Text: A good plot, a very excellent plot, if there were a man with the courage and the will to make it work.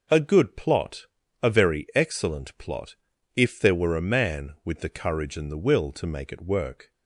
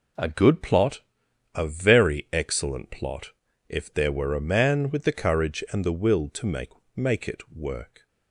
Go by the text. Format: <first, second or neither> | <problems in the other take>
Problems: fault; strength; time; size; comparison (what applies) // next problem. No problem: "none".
first | says "make" twice; at 6.9 s